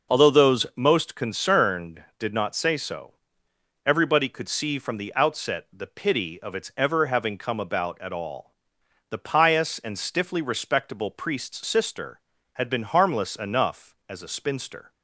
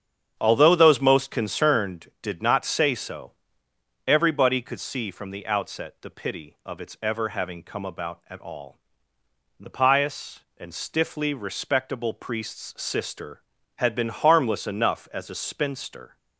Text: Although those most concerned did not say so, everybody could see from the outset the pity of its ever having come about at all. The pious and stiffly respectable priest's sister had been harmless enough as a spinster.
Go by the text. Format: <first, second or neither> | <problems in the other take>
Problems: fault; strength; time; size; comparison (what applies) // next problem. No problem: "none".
first | starts louder than the rest; strong; until 1.9 s; 8 dB